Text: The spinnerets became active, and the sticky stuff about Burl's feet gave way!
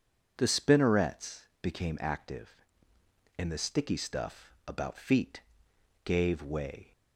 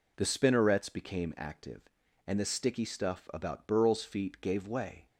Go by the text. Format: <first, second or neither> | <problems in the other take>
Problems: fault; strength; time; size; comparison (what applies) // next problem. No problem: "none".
second | pauses between "spinnerets" and "became"; slight; at 1.4 s; 0.18 s long // skips "Burl's"; at 4.9 s // pauses between "feet" and "gave"; noticeable; at 5.3 s; 0.64 s long